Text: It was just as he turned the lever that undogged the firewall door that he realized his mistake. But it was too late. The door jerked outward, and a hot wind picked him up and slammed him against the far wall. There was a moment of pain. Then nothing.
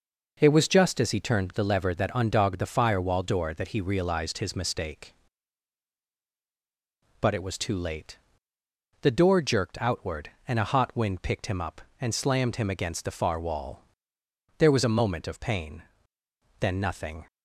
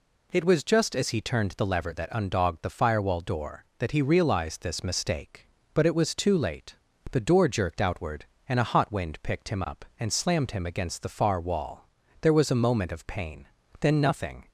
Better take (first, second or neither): first